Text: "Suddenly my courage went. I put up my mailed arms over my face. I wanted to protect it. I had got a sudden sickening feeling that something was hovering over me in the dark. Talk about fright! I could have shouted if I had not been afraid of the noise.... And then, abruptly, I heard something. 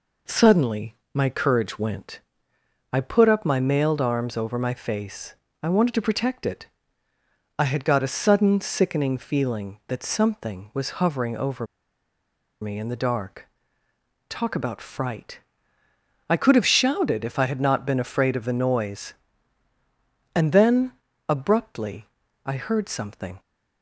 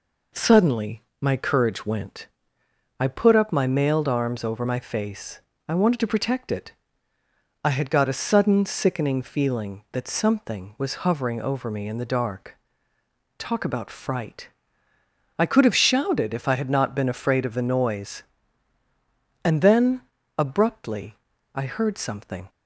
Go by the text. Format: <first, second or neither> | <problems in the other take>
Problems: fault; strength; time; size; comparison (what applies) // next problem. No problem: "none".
second | pauses between "Suddenly" and "my"; slight; at 0.9 s; 0.18 s long; slight in the second // pauses between "over" and "me"; noticeable; at 11.6 s; 0.96 s long